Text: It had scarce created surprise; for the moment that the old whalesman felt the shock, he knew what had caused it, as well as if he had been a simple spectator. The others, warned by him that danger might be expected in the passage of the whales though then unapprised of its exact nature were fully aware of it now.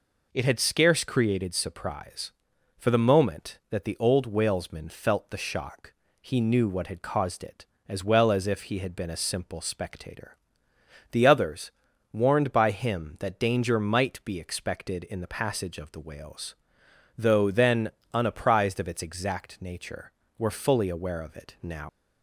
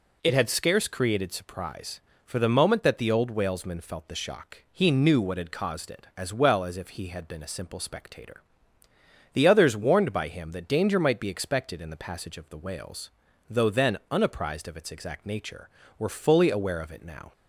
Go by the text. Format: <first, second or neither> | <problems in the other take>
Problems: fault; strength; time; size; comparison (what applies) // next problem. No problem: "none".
second | pauses between "whales" and "though"; noticeable; at 16.5 s; 0.62 s long; also in the second // pauses between "then" and "unapprised"; slight; at 17.9 s; 0.24 s long // leaves "now" unfinished; at 21.8 s; 155 ms